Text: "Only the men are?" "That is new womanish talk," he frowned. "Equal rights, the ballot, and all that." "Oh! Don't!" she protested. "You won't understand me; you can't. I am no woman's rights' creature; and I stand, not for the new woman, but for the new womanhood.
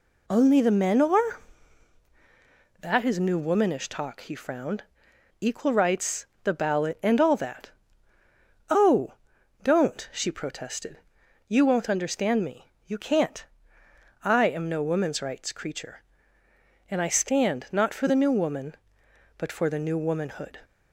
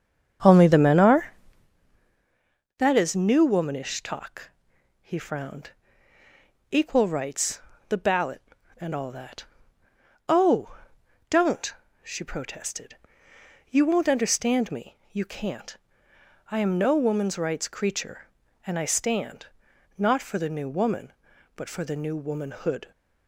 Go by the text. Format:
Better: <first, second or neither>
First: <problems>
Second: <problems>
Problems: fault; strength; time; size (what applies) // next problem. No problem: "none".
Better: first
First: none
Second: starts louder than the rest; strong; until 1.7 s; 7.5 dB